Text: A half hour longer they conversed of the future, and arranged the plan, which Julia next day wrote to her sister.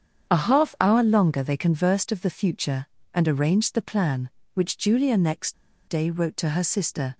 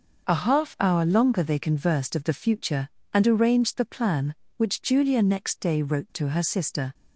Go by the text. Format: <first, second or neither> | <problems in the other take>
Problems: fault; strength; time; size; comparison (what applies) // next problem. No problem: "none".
second | starts louder than the rest; strong; until 1.3 s; 8 dB // pauses between "next" and "day"; slight; at 5.5 s; 0.33 s long